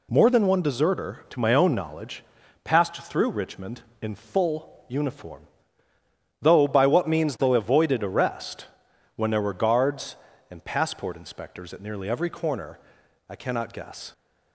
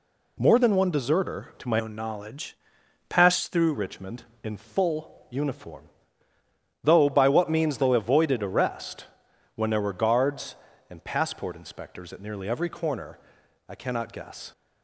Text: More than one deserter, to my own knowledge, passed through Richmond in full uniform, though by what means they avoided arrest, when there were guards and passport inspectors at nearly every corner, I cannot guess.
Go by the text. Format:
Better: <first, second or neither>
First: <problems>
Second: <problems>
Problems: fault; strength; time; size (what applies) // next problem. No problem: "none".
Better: first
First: none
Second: changes voice from "own" to "through"; from 1.7 to 3.7 s; 2.0 s long